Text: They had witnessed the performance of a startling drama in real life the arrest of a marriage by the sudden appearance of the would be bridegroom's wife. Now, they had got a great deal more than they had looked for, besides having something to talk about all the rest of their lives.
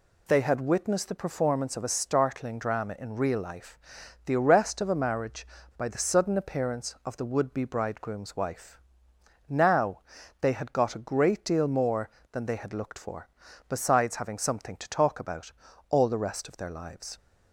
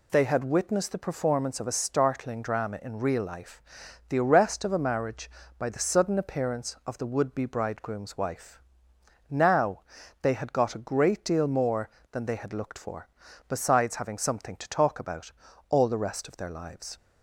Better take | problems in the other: neither | pauses between "life" and "the"; noticeable; the same in both // pauses between "about" and "all"; the same in both

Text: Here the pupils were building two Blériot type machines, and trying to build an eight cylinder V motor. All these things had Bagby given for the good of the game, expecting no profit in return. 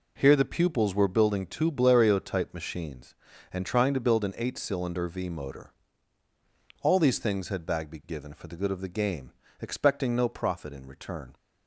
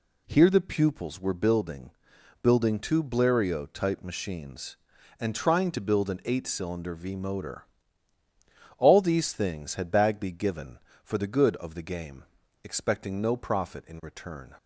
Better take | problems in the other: first | says "building" twice; at 2.4 s

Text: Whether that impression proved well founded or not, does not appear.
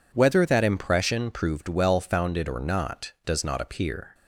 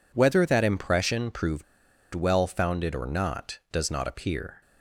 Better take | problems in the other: first | pauses between "proved" and "well"; noticeable; at 1.6 s; 0.50 s long

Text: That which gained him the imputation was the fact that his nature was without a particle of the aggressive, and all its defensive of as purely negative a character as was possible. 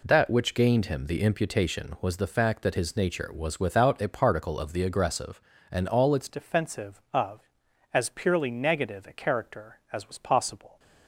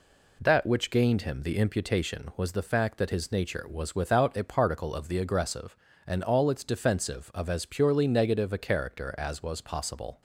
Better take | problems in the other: second | changes voice at "defensive"; from 6.2 s on; 4.5 s long

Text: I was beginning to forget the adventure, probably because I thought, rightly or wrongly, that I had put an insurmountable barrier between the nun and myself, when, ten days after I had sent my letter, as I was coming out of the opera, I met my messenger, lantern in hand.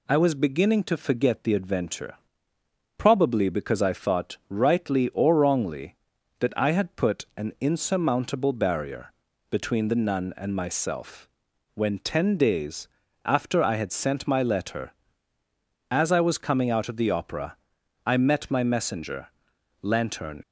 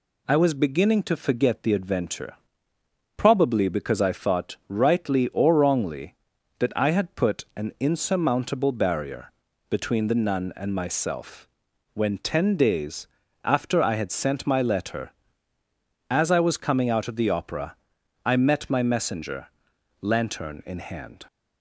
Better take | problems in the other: second | pauses between "barrier" and "between"; at 9.1 s; 0.38 s long; also in the second // pauses between "days" and "after"; at 12.8 s; 0.38 s long; also in the second // stops before "in hand"; at 20.4 s

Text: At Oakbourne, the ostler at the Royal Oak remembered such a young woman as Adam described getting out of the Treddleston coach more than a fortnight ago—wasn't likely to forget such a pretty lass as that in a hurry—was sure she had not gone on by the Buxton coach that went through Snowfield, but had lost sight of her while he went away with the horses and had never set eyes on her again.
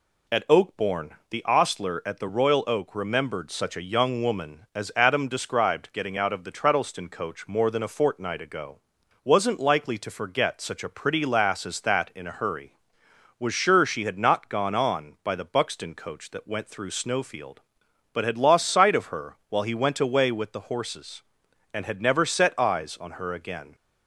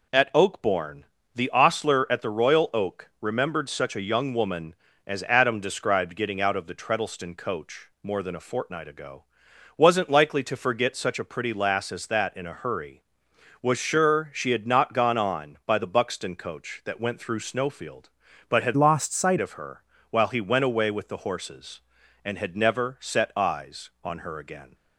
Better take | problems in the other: first | changes voice from "lost" to "sight"; from 18.7 to 19.3 s; 0.6 s long // pauses between "her" and "while"; slight; at 19.8 s; 0.30 s long; slight in the first

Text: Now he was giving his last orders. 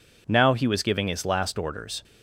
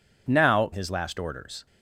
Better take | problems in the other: first | skips "he was giving"; at 0.7 s

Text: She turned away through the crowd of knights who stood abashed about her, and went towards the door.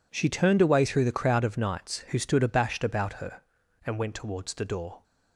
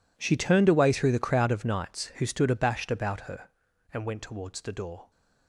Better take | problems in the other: first | gets quieter; strong; throughout; 18.5 dB

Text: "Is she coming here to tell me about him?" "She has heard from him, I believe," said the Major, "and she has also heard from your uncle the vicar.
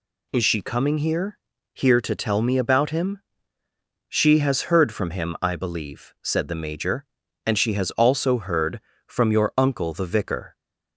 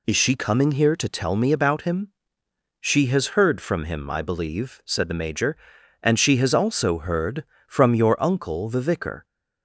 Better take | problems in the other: second | says "here" twice; at 1.7 s

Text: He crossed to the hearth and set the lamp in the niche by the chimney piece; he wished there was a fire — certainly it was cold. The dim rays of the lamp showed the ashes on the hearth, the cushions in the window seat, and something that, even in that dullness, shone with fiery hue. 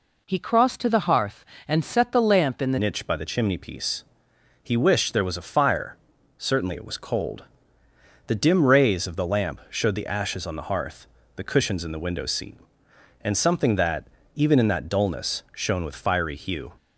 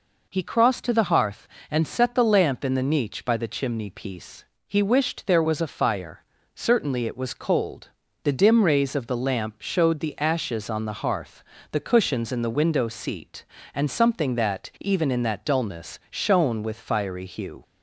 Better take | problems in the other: second | changes voice at "niche"; from 2.8 s on; 13.9 s long

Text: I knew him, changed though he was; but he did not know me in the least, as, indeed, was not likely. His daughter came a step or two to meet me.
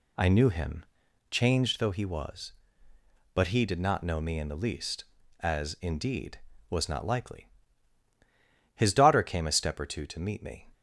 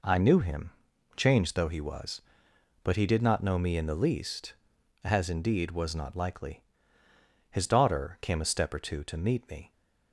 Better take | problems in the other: neither | none

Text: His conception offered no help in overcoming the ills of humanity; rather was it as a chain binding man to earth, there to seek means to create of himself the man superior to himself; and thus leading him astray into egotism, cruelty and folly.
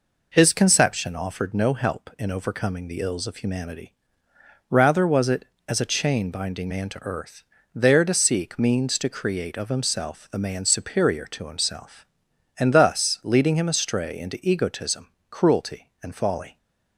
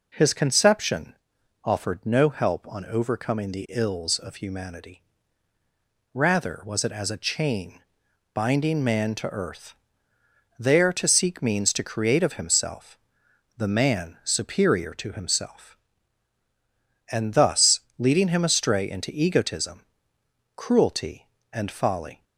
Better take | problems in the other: first | pauses between "conception" and "offered"; noticeable; at 1.1 s; 0.50 s long // says "on" for "in"; at 2.6 s // pauses between "chain" and "binding"; noticeable; at 7.8 s; 0.52 s long // pauses between "himself" and "the"; noticeable; at 12.9 s; 0.60 s long // pauses between "thus" and "leading"; slight; at 17.8 s; 0.16 s long

